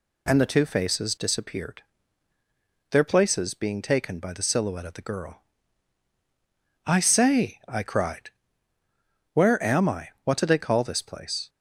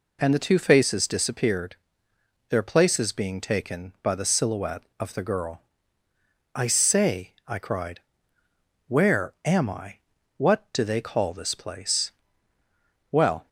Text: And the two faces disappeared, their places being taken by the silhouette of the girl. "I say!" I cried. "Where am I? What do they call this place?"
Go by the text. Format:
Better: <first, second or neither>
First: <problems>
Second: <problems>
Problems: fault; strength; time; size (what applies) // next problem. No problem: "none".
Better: first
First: none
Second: goes on to say "Well"; slight; from 13.1 s on; 0.36 s long